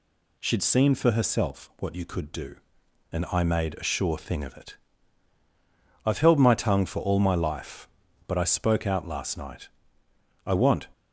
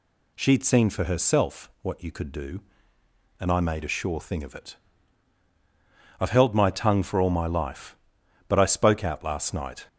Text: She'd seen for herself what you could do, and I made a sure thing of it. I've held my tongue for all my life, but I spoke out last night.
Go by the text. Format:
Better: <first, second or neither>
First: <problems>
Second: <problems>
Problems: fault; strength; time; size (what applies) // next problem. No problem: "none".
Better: second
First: goes on to say "I want"; slight; from 10.4 s on; 0.42 s long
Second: none